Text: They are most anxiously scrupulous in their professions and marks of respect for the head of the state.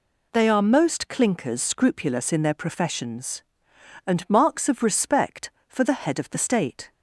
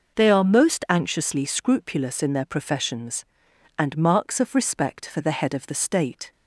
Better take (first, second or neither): second